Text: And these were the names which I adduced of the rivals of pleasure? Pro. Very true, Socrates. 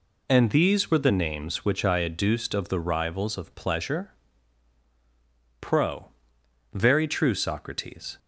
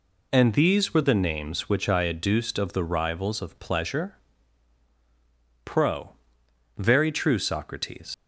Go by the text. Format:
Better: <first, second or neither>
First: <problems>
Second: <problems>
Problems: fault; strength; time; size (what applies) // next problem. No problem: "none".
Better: first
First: none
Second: leaves "Socrates" unfinished; at 8.1 s; 80 ms